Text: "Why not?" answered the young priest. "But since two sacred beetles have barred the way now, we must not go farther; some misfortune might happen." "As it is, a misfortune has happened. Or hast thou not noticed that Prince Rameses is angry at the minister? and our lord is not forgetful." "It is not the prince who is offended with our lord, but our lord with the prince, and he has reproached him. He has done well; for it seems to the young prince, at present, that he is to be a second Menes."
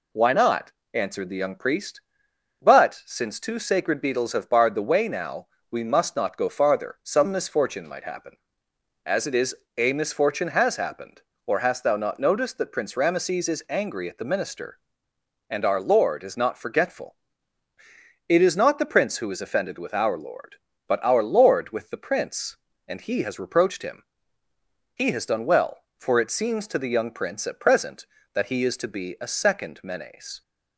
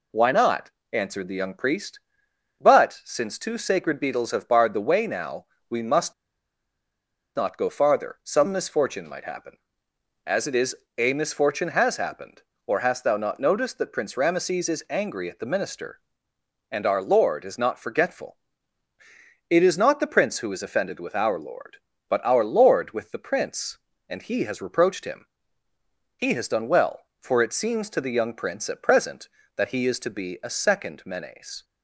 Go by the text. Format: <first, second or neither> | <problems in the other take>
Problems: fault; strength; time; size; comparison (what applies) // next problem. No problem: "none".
first | pauses between "must" and "not"; at 6.1 s; 1.2 s long